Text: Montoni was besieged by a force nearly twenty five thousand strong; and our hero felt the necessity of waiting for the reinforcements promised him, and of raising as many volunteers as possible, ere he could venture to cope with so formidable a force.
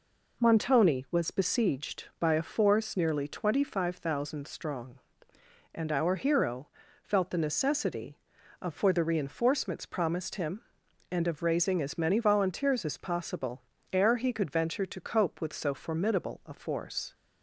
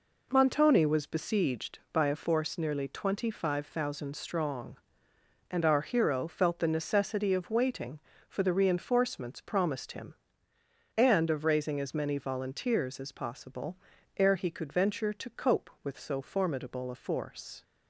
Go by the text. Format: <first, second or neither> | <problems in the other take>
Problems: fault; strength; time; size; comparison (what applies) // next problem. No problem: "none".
second | pauses between "hero" and "felt"; slight; at 6.6 s; 0.34 s long // skips "waiting"; at 8.7 s